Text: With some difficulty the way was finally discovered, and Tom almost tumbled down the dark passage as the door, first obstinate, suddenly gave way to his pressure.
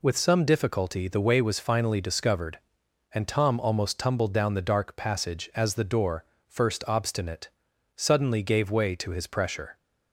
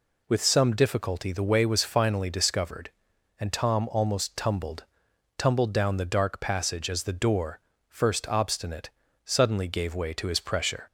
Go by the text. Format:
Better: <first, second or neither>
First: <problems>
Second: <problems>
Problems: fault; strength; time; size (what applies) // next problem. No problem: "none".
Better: first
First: none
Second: says "tumbled" twice; at 5.3 s